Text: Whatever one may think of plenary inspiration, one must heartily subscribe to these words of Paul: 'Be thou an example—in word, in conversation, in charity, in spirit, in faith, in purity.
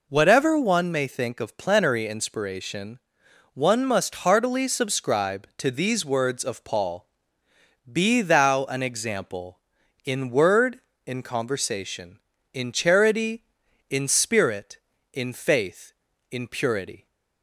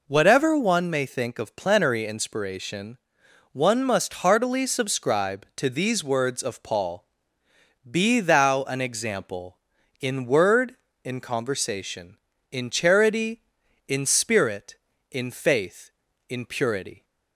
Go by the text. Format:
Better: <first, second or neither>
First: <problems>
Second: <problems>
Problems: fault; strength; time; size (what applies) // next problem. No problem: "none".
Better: neither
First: none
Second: none